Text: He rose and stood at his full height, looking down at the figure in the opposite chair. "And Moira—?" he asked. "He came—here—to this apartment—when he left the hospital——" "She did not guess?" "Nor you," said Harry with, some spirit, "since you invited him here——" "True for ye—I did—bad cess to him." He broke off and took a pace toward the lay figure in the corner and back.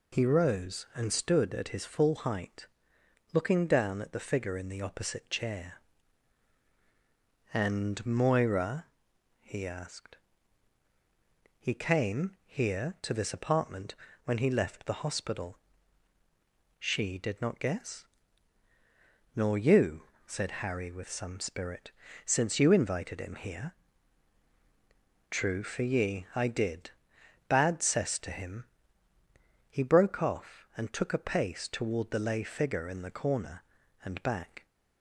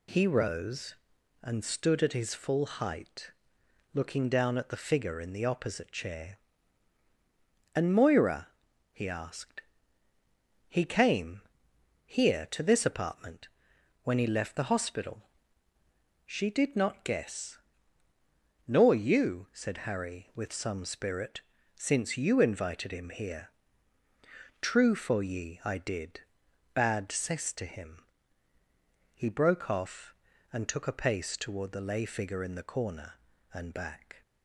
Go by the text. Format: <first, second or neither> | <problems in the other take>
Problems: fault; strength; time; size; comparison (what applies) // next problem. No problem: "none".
neither | none